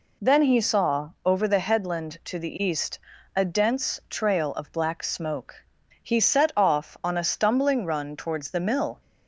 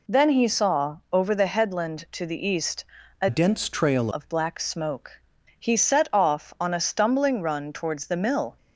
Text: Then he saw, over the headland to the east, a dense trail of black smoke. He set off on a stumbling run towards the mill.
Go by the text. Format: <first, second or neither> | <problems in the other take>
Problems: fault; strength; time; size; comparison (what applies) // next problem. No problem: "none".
first | changes voice from "dense" to "trail"; from 3.2 to 4.0 s; 0.8 s long